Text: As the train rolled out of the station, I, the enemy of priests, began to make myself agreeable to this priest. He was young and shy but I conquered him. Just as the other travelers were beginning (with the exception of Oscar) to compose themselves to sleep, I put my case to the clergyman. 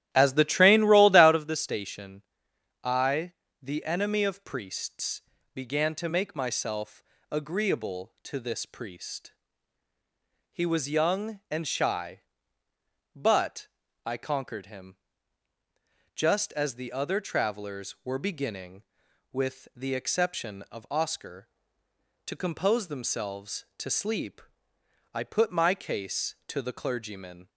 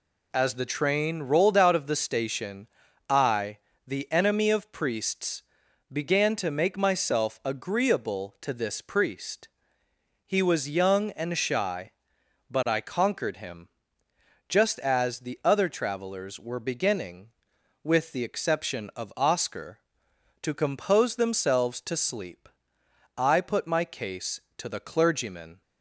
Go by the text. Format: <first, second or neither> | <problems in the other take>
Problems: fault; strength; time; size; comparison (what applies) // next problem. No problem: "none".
second | starts louder than the rest; strong; until 1.5 s; 12.5 dB // pauses between "myself" and "agreeable"; slight; at 7.0 s; 0.28 s long // pauses between "but" and "I"; at 13.6 s; 0.40 s long